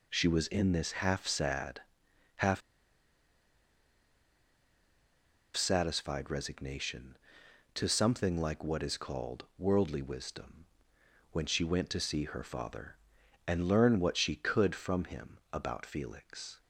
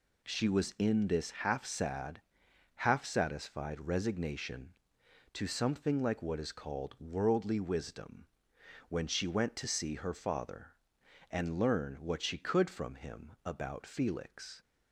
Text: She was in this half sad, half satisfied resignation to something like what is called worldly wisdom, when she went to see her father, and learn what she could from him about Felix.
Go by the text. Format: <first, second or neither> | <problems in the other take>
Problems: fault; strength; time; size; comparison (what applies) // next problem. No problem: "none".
second | pauses between "half" and "satisfied"; strong; at 2.6 s; 2.9 s long